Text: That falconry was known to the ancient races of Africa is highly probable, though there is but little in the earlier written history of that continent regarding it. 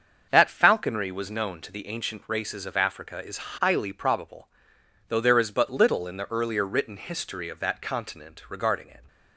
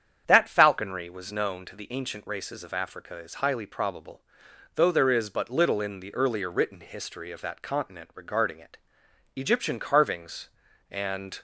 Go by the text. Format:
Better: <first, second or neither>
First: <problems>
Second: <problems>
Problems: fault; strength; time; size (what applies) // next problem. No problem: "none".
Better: first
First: starts louder than the rest; until 1.3 s; 7 dB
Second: starts louder than the rest; strong; until 1.2 s; 8.5 dB // goes on to say "Egyptian carvings and"; strong; from 9.3 s on; 2.0 s long